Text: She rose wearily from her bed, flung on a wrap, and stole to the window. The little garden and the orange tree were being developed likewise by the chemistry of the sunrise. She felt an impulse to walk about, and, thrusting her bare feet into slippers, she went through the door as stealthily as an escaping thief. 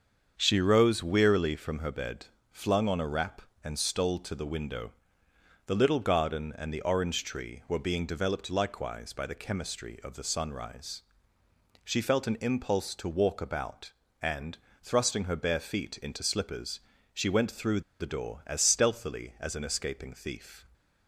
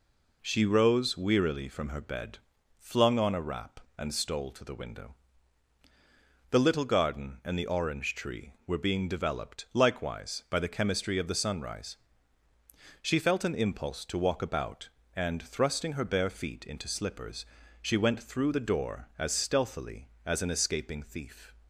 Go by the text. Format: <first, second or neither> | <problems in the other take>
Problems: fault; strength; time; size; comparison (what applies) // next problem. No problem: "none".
second | starts louder than the rest; strong; until 1.3 s; 7 dB // pauses between "through" and "the"; slight; at 17.8 s; 0.19 s long